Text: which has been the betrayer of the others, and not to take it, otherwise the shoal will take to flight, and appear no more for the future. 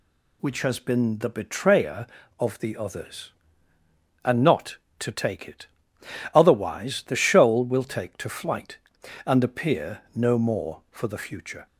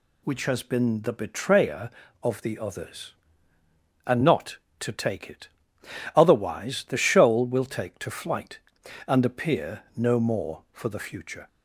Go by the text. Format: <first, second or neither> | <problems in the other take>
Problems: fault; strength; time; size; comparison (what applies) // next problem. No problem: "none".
neither | none